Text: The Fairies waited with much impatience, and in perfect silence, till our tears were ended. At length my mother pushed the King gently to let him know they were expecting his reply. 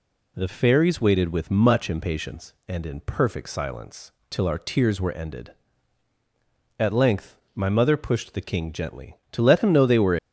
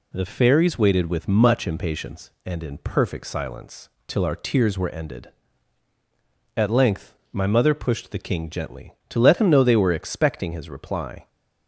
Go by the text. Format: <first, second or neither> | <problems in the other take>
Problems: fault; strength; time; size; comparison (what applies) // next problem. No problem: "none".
second | pauses between "length" and "my"; slight; at 7.3 s; 0.18 s long; slight in the second // stops before "expecting his reply"; at 10.1 s